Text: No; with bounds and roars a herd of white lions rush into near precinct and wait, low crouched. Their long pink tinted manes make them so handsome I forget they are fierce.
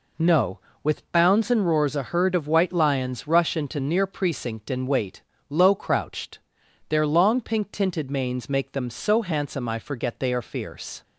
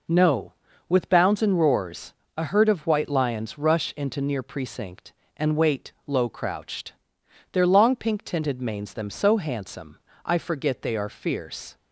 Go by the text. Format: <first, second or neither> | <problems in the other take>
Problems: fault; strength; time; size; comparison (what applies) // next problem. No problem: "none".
first | pauses between "roars" and "a"; slight; at 2.1 s; 0.24 s long // skips "make"; at 8.9 s // pauses between "handsome" and "I"; slight; at 10.0 s; 0.24 s long